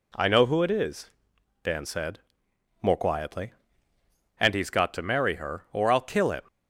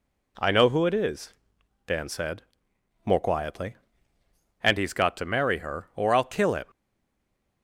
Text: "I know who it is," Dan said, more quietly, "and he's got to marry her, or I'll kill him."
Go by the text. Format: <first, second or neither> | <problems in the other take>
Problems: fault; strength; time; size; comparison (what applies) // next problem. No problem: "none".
first | stays silent after the last word; slight; from 6.6 s on; 1.0 s long